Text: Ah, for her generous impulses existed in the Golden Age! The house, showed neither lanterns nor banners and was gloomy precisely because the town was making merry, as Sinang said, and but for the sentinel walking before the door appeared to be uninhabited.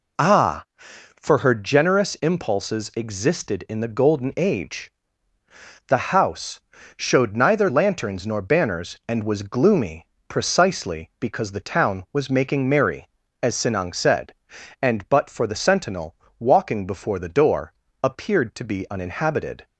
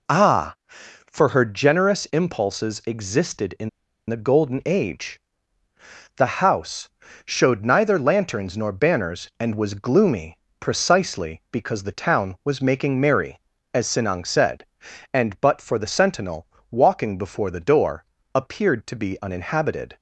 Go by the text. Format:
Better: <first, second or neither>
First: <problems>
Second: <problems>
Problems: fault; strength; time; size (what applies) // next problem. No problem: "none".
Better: first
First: pauses between "gloomy" and "precisely"; slight; at 10.0 s; 0.24 s long // pauses between "sentinel" and "walking"; slight; at 16.1 s; 0.24 s long // pauses between "door" and "appeared"; slight; at 17.7 s; 0.30 s long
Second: pauses between "in" and "the"; at 3.6 s; 0.40 s long // pauses between "gloomy" and "precisely"; slight; at 10.3 s; 0.24 s long // pauses between "sentinel" and "walking"; slight; at 16.4 s; 0.24 s long // pauses between "door" and "appeared"; slight; at 18.0 s; 0.30 s long